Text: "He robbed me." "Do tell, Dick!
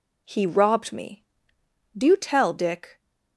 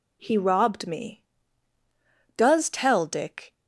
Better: first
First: none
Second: says "Does" for "Do"; at 2.3 s

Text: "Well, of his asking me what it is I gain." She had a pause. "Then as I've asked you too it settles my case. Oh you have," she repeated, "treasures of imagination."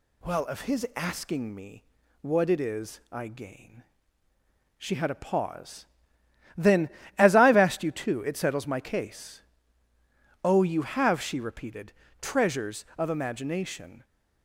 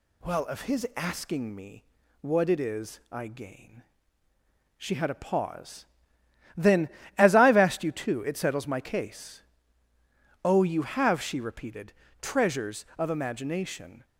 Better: neither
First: pauses between "me" and "what"; at 1.8 s; 0.38 s long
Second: pauses between "me" and "what"; at 1.8 s; 0.37 s long

